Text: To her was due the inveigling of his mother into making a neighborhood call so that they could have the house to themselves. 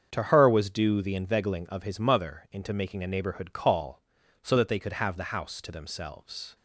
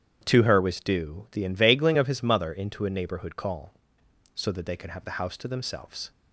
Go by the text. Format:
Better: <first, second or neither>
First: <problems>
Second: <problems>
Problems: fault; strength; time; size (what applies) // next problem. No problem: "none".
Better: first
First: starts louder than the rest; until 1.1 s; 7 dB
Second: starts louder than the rest; strong; until 1.2 s; 9.5 dB // skips "making"; at 2.8 s